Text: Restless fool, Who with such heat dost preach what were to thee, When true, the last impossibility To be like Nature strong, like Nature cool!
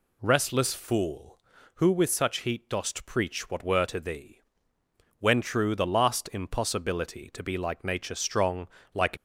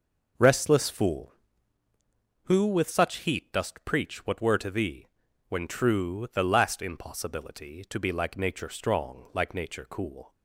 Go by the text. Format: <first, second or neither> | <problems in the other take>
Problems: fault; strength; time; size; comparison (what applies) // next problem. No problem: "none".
second | stops before "Nature cool"; at 9.1 s